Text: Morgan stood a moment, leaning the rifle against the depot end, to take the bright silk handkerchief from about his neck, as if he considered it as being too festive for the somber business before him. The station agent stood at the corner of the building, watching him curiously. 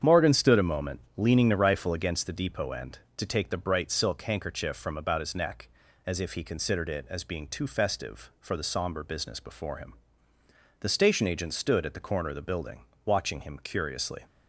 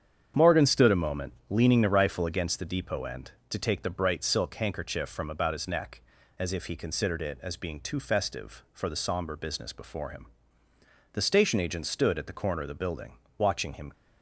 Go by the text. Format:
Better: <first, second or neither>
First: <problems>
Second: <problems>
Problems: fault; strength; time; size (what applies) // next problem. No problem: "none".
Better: first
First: starts louder than the rest; strong; until 1.2 s; 8 dB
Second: starts louder than the rest; strong; until 1.5 s; 8 dB // stops before "curiously"; at 13.9 s